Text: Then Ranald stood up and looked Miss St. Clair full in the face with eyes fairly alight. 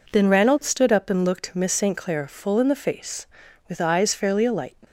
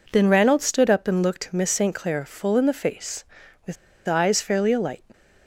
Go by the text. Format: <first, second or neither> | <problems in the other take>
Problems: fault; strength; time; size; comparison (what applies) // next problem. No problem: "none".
first | pauses between "with" and "eyes"; slight; at 3.7 s; 0.32 s long